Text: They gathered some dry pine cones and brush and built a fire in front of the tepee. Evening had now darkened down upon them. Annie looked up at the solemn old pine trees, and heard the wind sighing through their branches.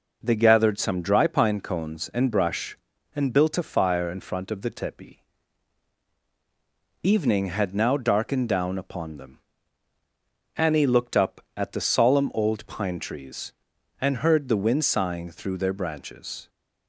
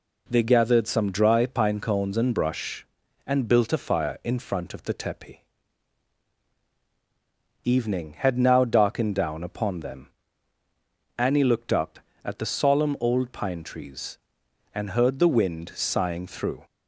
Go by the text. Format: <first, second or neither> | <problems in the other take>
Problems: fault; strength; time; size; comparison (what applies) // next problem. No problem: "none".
first | stops before "their branches"; at 16.6 s